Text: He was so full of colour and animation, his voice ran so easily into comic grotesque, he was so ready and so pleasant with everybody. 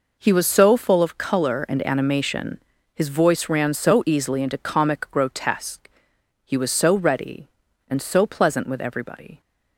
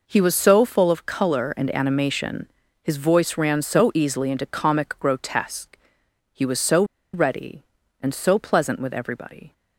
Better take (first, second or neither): first